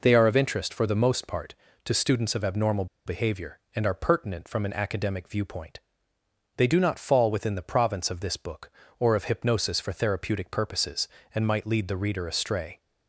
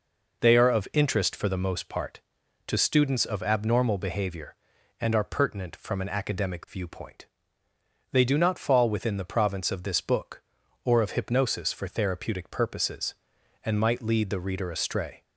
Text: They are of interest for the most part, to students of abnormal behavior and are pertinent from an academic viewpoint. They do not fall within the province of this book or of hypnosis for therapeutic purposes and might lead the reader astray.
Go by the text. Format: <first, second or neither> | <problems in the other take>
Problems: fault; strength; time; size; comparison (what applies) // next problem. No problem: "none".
second | pauses between "abnormal" and "behavior"; slight; at 2.8 s; 0.21 s long